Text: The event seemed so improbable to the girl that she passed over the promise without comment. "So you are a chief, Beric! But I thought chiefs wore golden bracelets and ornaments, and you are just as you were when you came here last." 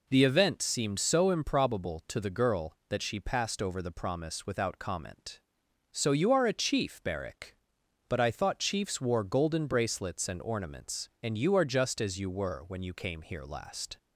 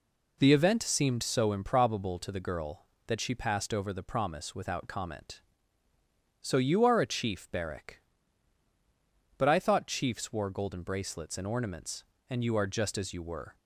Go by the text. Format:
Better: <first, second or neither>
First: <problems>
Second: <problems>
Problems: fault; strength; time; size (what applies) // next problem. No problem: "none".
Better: first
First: none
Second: stops before "when you came here last"; at 13.5 s